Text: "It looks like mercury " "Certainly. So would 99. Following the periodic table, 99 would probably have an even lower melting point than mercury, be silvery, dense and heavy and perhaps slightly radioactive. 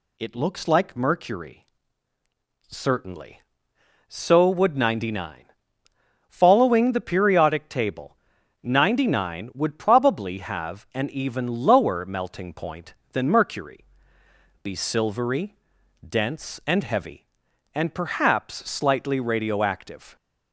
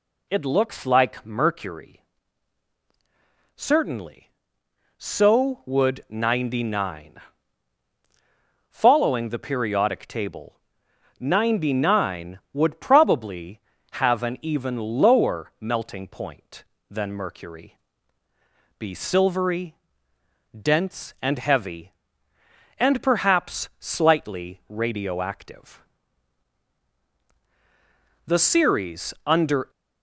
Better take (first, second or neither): first